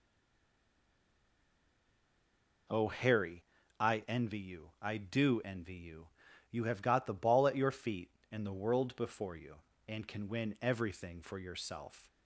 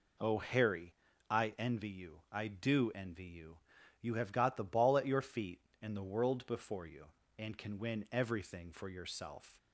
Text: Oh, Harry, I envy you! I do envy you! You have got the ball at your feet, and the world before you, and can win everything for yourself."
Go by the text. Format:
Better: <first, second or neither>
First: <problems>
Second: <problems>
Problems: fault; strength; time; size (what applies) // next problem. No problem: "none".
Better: second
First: stays silent before the first word; strong; until 2.6 s; 2.6 s long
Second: none